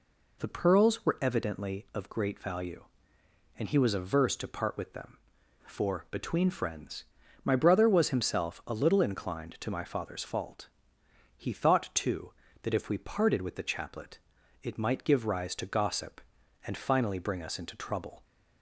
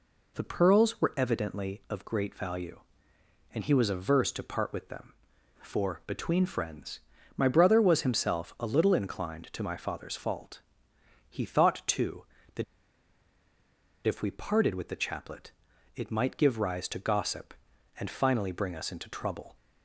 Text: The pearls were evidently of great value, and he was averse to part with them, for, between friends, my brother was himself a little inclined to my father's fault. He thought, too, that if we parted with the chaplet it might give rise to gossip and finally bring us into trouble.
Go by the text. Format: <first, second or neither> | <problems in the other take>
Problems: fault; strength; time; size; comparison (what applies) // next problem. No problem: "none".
first | pauses between "that" and "if"; strong; at 12.6 s; 1.4 s long // pauses between "chaplet" and "it"; at 15.5 s; 0.44 s long; also in the first